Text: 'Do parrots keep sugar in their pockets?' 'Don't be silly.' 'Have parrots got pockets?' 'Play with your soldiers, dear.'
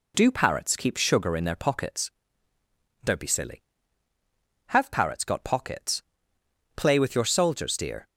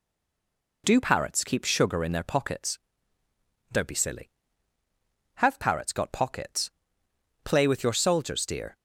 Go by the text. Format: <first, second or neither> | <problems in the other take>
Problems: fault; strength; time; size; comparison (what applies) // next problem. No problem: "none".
first | stays silent before the first word; slight; until 0.8 s; 0.8 s long